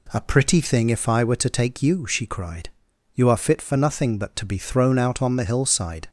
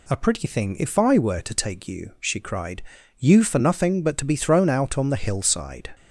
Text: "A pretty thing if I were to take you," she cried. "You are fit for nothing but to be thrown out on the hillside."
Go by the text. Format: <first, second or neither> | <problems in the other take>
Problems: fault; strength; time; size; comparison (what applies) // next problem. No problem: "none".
first | skips "are fit"; at 3.4 s